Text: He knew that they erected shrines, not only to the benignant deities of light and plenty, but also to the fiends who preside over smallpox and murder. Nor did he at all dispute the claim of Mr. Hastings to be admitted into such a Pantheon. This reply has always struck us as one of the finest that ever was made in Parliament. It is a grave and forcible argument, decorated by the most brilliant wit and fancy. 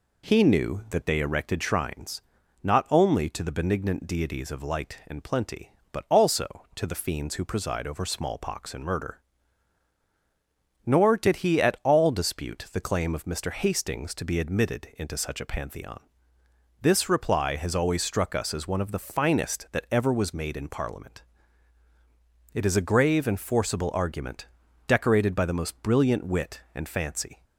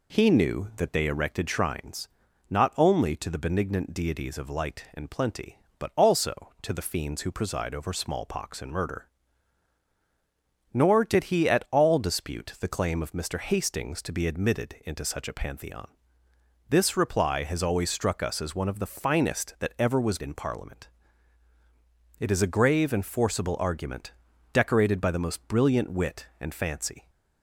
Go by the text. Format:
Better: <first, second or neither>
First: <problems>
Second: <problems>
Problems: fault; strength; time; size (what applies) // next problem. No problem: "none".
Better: first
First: none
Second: skips "made"; at 20.2 s